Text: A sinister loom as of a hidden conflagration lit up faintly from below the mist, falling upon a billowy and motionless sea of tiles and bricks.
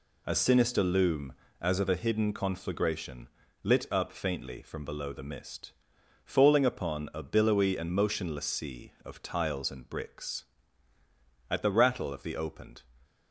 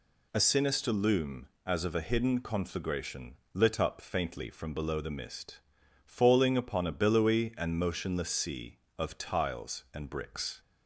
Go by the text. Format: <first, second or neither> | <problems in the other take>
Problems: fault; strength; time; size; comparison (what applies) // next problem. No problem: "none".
second | pauses between "conflagration" and "lit"; slight; at 3.2 s; 0.34 s long; slight in the second // goes on to say "At the rattle of the opened"; from 11.4 s on; 1.3 s long